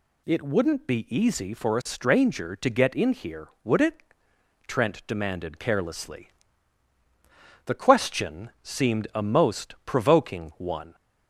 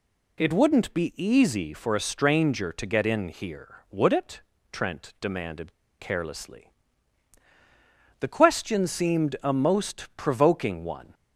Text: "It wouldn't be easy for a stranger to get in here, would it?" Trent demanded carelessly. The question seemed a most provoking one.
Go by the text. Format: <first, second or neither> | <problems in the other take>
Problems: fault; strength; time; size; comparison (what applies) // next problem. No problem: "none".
first | pauses between "demanded" and "carelessly"; slight; at 5.7 s; 0.26 s long